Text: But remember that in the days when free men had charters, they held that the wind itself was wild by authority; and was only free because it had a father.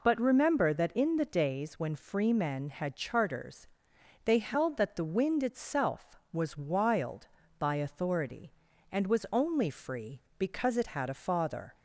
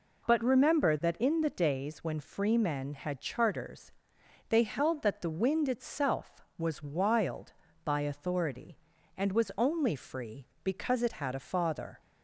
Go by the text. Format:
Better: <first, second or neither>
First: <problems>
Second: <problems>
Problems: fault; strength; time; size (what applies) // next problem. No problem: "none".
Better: neither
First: none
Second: none